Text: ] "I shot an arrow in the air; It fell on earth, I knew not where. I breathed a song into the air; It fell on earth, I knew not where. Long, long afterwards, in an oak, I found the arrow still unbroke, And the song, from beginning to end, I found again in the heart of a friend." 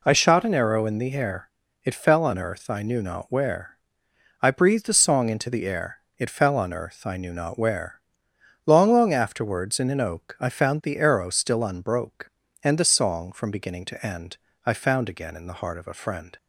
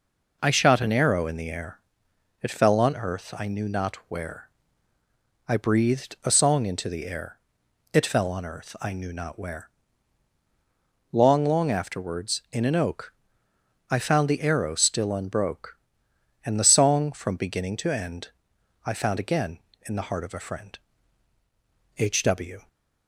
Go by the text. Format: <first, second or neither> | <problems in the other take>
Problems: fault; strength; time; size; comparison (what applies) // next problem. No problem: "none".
first | goes on to say "H W"; noticeable; from 21.9 s on; 0.70 s long